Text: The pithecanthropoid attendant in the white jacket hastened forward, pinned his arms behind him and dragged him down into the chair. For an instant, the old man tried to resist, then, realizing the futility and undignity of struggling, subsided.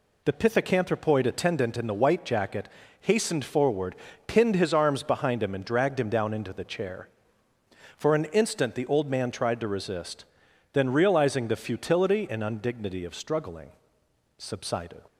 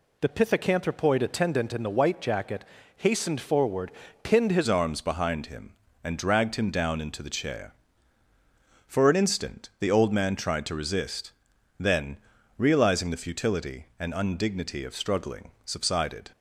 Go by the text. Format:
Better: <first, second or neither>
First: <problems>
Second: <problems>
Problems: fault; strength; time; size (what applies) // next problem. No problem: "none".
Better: first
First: pauses between "jacket" and "hastened"; slight; at 2.6 s; 0.32 s long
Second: pauses between "jacket" and "hastened"; slight; at 2.6 s; 0.32 s long // changes voice at "arms"; from 4.6 s on; 11.7 s long